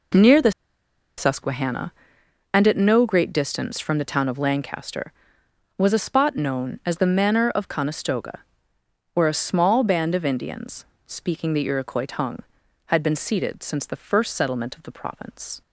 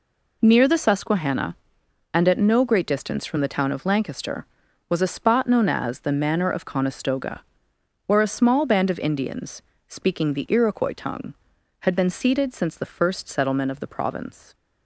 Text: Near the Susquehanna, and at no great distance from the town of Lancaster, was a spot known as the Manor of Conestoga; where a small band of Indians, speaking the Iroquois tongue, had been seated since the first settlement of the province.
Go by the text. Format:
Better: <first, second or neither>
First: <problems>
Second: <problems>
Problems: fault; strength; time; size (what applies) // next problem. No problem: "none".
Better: second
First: pauses between "the" and "Susquehanna"; noticeable; at 0.5 s; 0.67 s long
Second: none